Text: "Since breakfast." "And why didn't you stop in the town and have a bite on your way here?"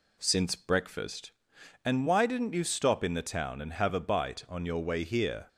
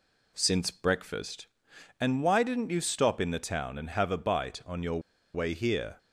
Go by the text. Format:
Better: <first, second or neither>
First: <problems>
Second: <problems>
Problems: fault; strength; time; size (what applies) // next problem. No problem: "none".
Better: first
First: none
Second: pauses between "your" and "way"; slight; at 4.9 s; 0.34 s long